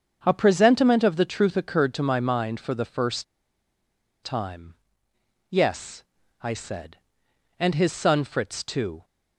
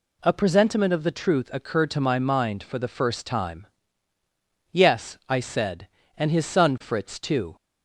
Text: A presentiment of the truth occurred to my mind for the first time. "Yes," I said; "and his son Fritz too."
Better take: second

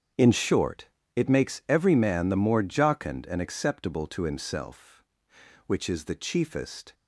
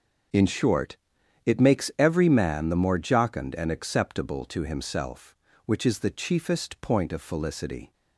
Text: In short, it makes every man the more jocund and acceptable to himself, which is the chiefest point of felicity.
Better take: second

